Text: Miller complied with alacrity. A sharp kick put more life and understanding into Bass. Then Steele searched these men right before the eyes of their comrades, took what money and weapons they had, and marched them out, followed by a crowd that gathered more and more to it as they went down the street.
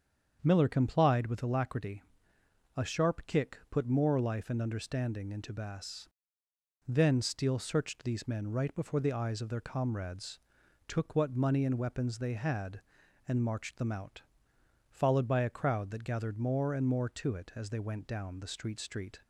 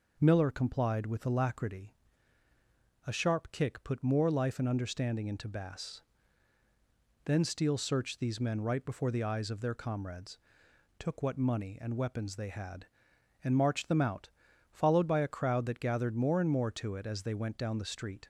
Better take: second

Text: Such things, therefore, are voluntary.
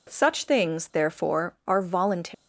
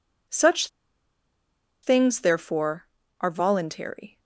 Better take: first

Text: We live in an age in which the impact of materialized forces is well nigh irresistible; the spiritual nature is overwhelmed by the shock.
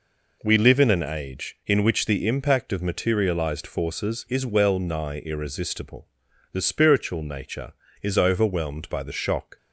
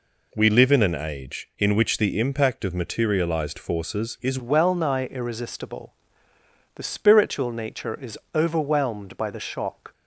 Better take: first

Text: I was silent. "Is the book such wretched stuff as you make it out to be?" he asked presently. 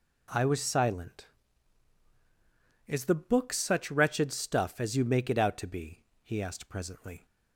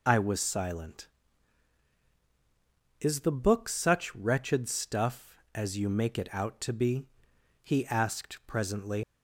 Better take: first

